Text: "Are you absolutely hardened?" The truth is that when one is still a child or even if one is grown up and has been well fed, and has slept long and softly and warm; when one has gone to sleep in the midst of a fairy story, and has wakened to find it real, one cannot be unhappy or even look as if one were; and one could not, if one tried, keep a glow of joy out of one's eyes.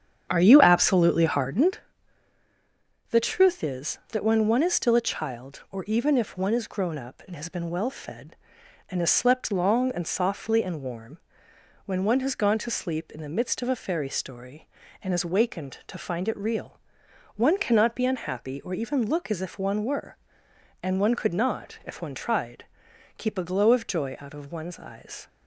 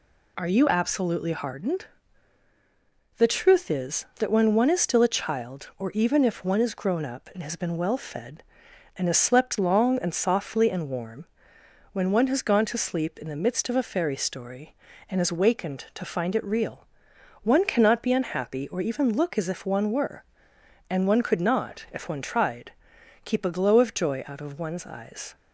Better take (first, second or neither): second